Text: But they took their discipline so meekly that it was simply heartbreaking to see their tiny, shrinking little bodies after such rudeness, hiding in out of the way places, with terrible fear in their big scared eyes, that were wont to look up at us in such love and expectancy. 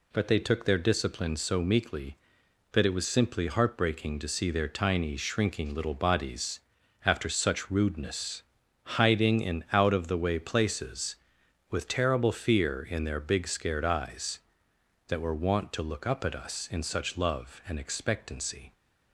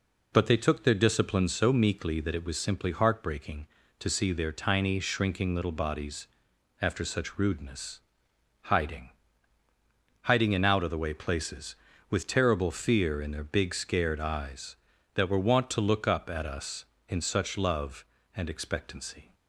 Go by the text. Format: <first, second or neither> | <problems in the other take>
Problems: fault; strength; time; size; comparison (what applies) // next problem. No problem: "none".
first | pauses between "bodies" and "after"; noticeable; at 6.2 s; 0.56 s long; noticeable in the first // says "hiding" twice; at 10.2 s